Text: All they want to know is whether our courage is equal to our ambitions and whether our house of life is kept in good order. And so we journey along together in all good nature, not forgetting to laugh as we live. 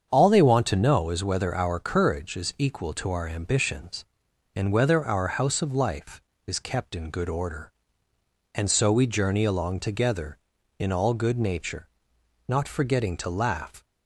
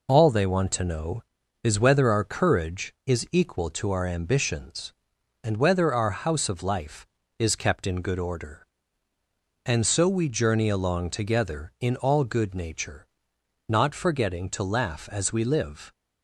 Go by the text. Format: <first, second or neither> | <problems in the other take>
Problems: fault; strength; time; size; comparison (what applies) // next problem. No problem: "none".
second | starts louder than the rest; strong; until 1.1 s; 7.5 dB // stops before "as we live"; at 13.8 s